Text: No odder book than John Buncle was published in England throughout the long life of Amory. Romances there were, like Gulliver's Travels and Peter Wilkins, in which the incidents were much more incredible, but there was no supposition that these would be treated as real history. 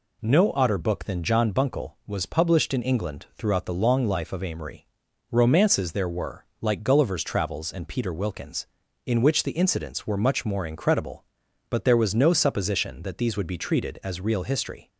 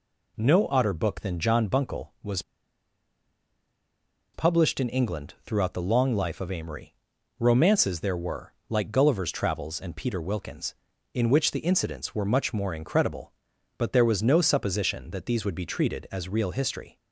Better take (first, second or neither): first